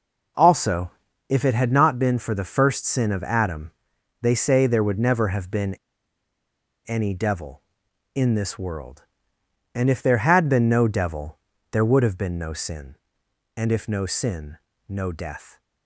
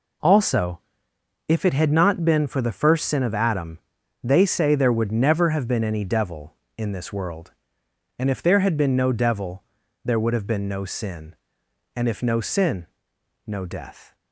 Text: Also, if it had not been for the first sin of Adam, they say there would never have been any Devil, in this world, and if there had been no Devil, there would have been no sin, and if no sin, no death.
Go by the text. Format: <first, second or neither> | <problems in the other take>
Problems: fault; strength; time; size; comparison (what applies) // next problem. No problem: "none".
second | pauses between "been" and "any"; at 5.7 s; 1.1 s long